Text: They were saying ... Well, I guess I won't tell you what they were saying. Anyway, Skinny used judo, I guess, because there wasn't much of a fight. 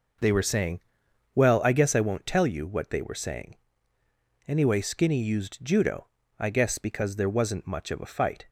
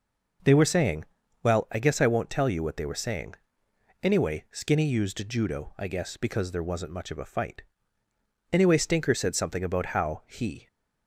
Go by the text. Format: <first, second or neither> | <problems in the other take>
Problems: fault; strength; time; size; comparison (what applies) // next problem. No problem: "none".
first | goes on to say "Anyway Stinker said something about how he"; strong; from 8.5 s on; 2.1 s long